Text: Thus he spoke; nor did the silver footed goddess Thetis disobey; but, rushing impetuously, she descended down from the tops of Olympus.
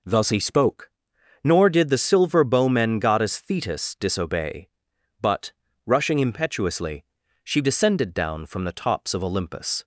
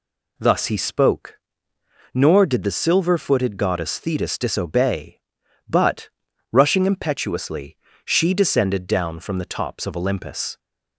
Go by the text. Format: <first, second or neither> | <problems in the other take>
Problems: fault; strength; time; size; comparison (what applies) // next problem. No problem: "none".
second | says "bowmen" for "footed"; at 2.4 s